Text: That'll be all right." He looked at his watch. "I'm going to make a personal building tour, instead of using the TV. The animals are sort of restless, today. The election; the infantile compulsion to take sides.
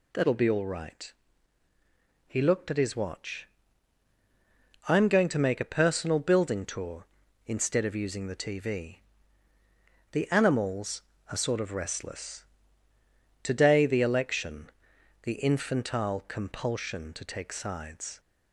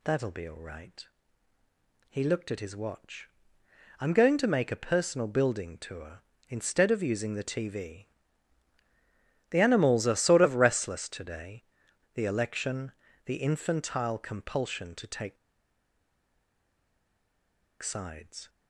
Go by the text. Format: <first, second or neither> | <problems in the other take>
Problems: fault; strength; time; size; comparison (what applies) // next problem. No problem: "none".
first | pauses between "take" and "sides"; strong; at 15.3 s; 2.4 s long